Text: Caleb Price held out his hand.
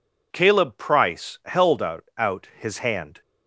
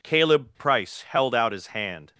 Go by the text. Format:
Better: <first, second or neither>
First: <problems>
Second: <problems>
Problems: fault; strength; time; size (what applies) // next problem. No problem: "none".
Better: second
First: says "out" twice; at 2.1 s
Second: none